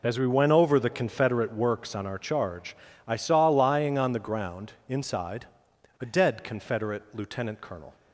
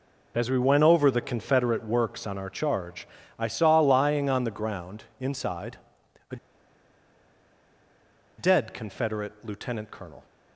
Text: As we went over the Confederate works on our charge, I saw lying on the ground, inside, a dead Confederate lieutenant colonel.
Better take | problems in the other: first | pauses between "a" and "dead"; strong; at 6.3 s; 2.0 s long

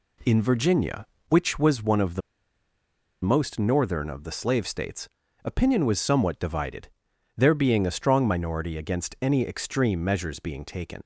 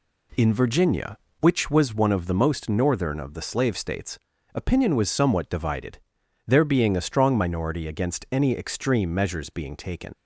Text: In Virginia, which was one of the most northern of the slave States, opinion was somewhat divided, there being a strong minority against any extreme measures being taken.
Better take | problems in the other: second | pauses between "the" and "most"; at 2.2 s; 1.0 s long

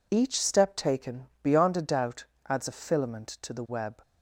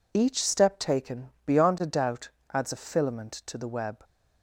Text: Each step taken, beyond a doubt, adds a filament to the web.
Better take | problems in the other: neither | none

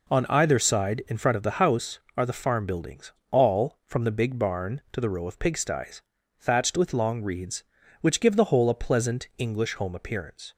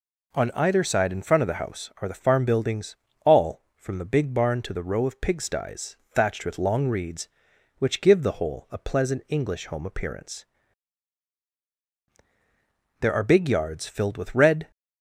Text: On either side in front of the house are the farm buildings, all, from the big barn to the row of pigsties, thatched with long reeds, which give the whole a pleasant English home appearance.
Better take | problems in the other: first | goes on to say "There are big yards filled with red"; strong; from 13.0 s on; 1.7 s long

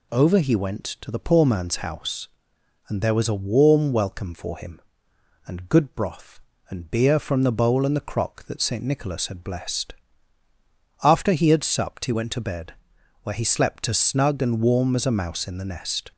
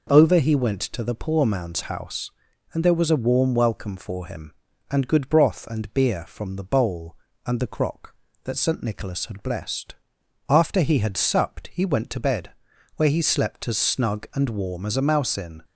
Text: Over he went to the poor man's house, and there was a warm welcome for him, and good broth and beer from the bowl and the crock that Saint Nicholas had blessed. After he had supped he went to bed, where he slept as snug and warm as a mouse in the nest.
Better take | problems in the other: first | stops before "the nest"; at 15.6 s

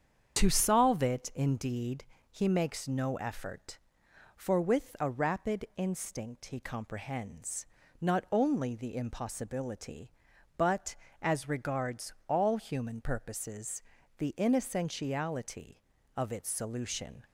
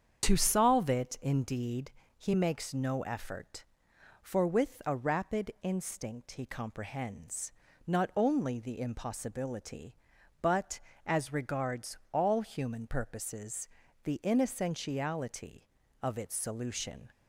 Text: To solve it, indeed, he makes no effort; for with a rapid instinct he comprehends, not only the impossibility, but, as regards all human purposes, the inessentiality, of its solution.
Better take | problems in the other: neither | starts louder than the rest; strong; the same in both

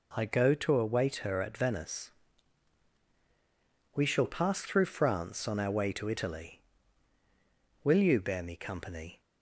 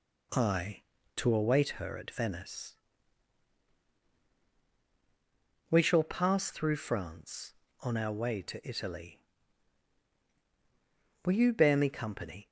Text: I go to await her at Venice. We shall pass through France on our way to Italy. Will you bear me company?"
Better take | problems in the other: first | skips "go"; at 0.9 s

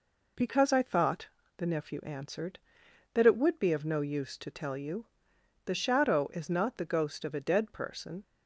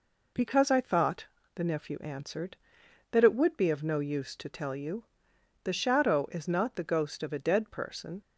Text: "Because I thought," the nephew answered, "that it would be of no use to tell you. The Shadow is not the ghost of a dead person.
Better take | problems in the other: neither | none

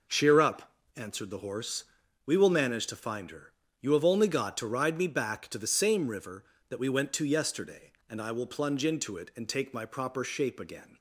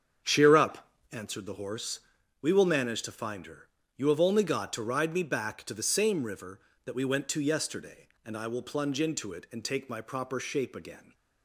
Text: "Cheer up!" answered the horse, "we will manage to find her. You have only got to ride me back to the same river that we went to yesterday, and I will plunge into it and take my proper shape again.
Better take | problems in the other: first | starts louder than the rest; strong; until 1.4 s; 7.5 dB

